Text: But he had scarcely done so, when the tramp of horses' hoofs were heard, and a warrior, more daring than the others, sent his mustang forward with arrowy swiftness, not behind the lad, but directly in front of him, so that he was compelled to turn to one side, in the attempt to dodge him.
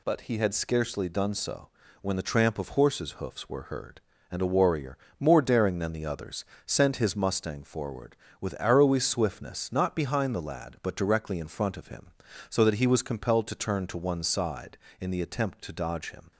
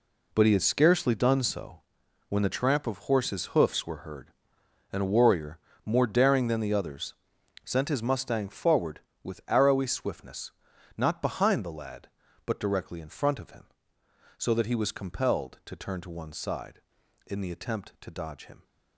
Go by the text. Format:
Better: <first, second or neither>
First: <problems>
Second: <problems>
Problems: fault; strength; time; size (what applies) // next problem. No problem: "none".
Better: first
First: none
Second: gets quieter; strong; throughout; 11 dB